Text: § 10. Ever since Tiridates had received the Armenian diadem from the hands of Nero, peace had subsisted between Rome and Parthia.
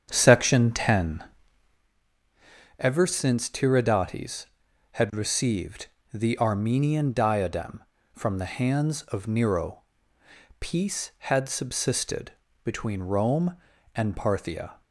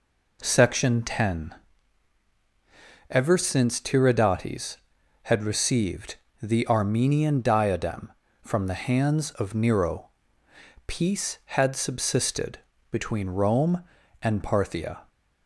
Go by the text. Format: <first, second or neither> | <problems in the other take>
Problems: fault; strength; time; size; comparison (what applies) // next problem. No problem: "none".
second | starts louder than the rest; strong; until 2.0 s; 8 dB // pauses between "received" and "the"; slight; at 5.8 s; 0.26 s long; slight in the second // pauses between "subsisted" and "between"; slight; at 12.3 s; 0.34 s long; slight in the second